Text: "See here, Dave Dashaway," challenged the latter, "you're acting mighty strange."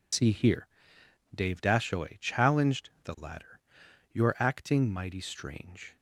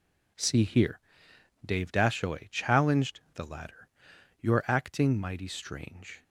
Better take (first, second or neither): second